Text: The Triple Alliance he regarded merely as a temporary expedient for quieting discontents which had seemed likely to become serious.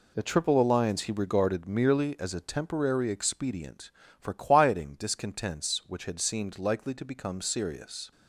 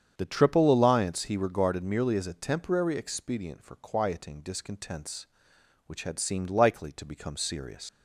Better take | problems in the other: first | starts louder than the rest; strong; until 1.1 s; 8 dB // leaves "serious" unfinished; at 7.8 s; 85 ms

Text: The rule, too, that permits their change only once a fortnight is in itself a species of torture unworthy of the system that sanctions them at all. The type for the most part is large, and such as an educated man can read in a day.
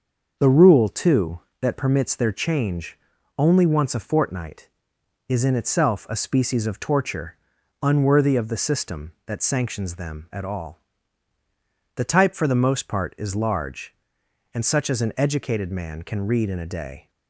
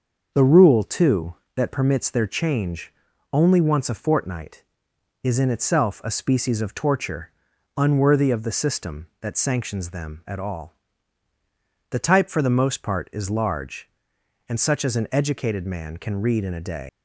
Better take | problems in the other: first | starts louder than the rest; until 1.3 s; 6.5 dB; also in the first // pauses between "change" and "only"; at 2.9 s; 0.40 s long; also in the first // pauses between "torture" and "unworthy"; noticeable; at 7.3 s; 0.46 s long; noticeable in the first // leaves "day" unfinished; at 16.8 s; 155 ms

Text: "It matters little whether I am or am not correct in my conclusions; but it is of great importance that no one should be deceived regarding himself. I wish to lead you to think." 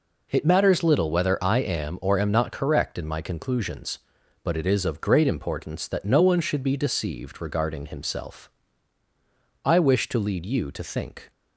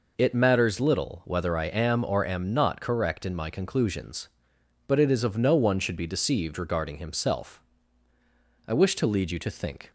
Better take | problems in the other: first | skips "great importance that"; at 5.3 s

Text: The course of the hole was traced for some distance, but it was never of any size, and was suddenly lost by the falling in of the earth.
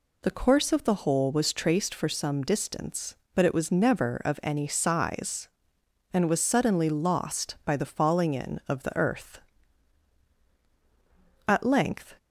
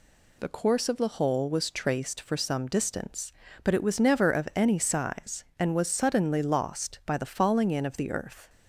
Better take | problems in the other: second | goes on to say "At length"; noticeable; from 11.4 s on; 0.70 s long

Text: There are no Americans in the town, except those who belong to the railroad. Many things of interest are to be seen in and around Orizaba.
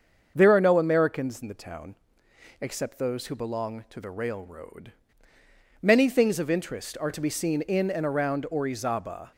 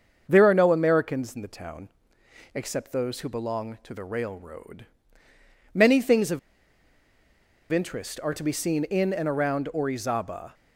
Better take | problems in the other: first | starts louder than the rest; until 1.2 s; 6.5 dB; also in the first // pauses between "of" and "interest"; strong; at 6.3 s; 1.3 s long

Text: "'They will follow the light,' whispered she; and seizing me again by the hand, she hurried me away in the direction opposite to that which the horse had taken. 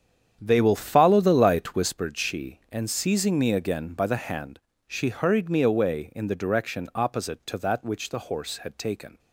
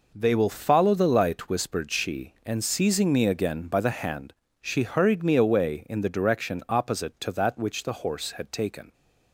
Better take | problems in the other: second | starts louder than the rest; strong; until 2.0 s; 8.5 dB

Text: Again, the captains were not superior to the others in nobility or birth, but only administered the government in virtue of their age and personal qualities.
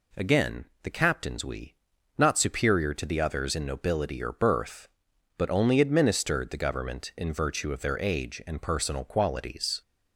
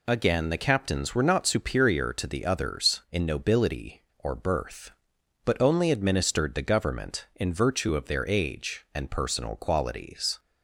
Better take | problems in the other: second | says "we" for "were"; at 1.4 s

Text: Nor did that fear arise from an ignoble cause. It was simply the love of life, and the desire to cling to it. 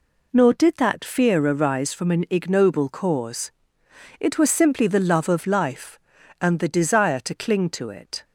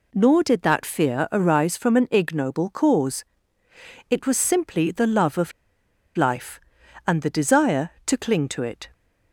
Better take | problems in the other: first | pauses between "of" and "life"; noticeable; at 5.5 s; 0.64 s long

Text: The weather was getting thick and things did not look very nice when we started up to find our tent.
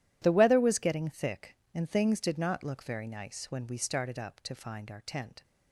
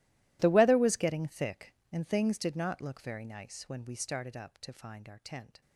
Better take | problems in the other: first | gets quieter; strong; throughout; 21.5 dB

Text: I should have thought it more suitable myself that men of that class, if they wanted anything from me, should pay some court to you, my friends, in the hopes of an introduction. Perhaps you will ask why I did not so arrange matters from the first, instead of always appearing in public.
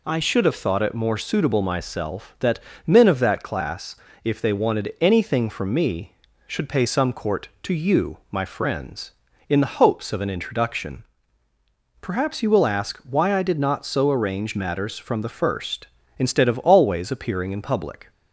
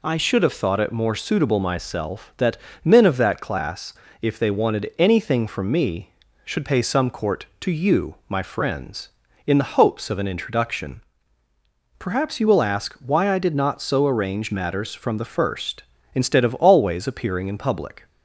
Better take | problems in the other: neither | pauses between "that" and "men"; slight; the same in both

